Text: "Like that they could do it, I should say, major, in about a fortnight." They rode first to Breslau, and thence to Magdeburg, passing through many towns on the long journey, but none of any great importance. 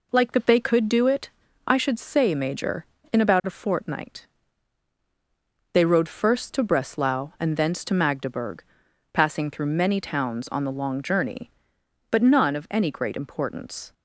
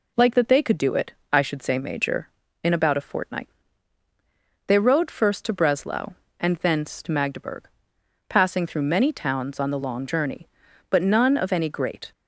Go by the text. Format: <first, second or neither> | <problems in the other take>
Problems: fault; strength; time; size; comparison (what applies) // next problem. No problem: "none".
first | stops before "importance"; at 12.1 s